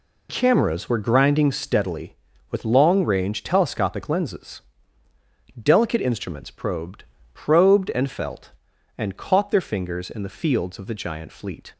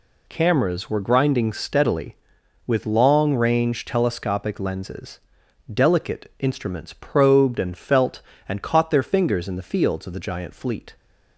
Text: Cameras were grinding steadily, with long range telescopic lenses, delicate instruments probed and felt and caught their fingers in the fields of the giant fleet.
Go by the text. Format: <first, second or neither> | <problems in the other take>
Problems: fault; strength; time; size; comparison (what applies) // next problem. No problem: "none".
second | says "probed" twice; at 7.3 s